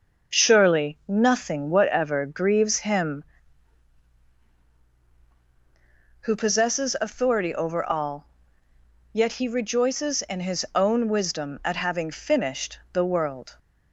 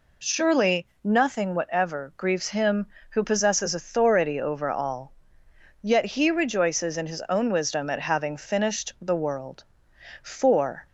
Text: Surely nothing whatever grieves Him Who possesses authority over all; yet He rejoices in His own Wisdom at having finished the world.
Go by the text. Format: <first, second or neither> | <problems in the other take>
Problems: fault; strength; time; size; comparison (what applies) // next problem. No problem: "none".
first | pauses between "Surely" and "nothing"; slight; at 0.8 s; 0.16 s long // goes on to say "For"; noticeable; from 10.2 s on; 0.64 s long